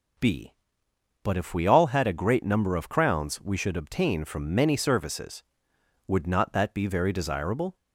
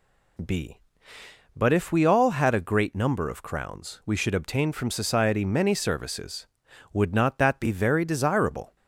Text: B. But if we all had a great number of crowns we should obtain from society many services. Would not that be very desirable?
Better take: second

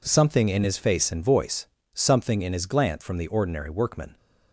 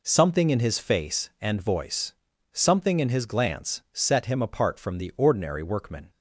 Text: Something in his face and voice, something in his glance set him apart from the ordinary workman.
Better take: second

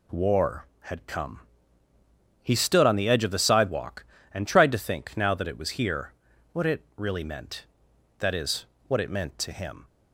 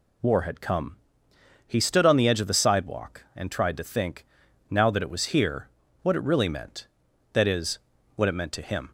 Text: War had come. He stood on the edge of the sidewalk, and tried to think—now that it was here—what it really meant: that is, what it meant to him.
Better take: neither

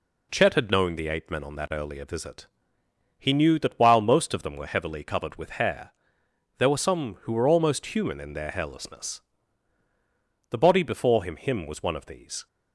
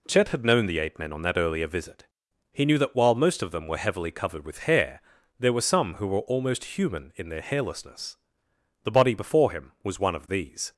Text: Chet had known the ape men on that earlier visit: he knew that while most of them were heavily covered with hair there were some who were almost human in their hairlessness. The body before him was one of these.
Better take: second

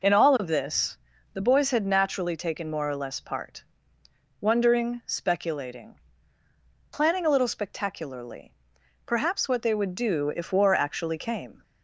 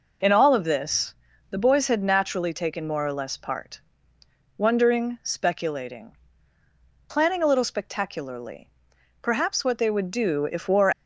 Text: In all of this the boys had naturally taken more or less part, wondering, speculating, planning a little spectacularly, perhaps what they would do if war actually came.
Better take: first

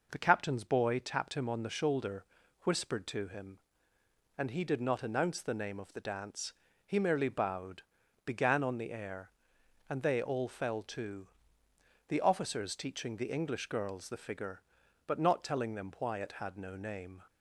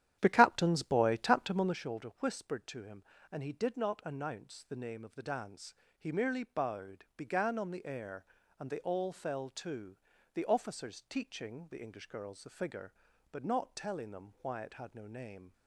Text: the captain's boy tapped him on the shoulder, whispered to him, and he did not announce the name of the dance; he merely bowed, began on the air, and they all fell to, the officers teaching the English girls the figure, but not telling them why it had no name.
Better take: first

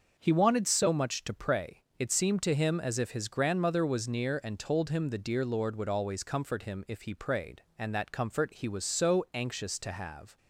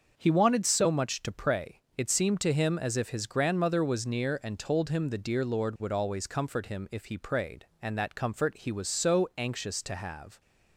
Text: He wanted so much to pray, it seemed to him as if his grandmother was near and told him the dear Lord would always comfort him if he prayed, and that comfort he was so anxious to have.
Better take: neither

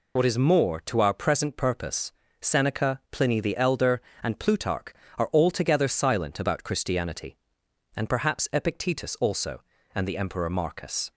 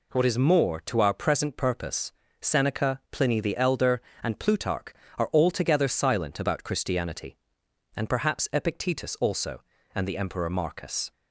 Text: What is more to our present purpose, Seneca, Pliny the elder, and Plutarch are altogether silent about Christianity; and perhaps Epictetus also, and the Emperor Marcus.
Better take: second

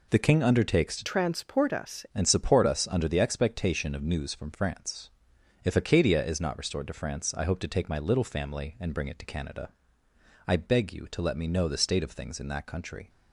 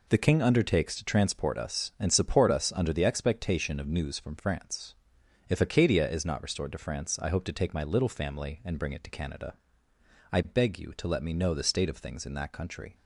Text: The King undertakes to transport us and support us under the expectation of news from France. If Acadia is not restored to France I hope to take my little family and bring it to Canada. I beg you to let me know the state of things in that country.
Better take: second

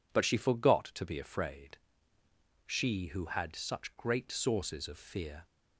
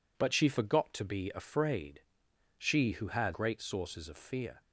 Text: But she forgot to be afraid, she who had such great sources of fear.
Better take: first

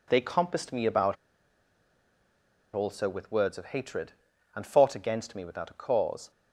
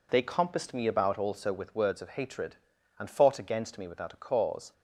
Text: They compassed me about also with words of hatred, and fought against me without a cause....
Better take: second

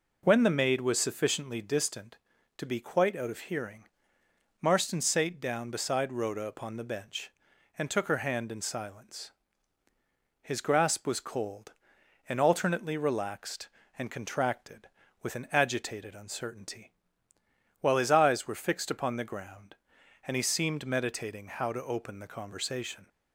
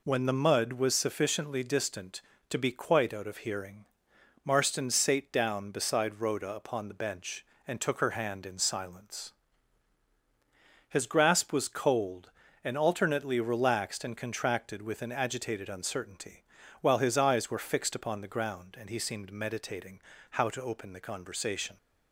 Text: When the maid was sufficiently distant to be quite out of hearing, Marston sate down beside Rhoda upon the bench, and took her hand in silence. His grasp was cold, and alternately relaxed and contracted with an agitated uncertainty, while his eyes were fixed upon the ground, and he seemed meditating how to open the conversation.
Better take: first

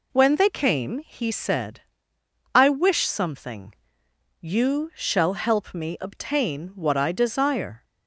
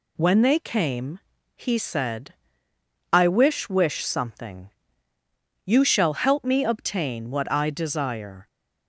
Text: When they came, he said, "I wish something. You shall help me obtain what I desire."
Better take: first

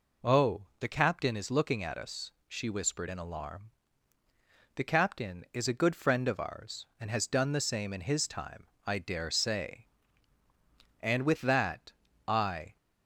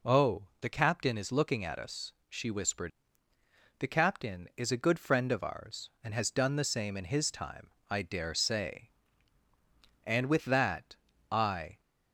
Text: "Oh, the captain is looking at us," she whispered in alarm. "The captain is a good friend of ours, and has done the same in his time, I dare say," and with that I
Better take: first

